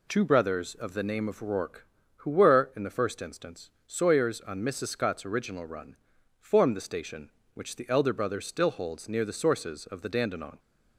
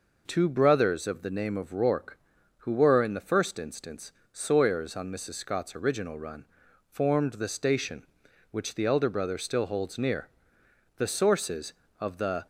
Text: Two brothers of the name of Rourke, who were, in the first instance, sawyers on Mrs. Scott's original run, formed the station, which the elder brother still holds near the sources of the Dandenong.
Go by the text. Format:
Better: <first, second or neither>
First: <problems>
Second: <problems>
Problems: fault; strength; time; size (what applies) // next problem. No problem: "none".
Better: first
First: none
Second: pauses between "near" and "the"; noticeable; at 10.2 s; 0.70 s long // stops before "Dandenong"; at 12.4 s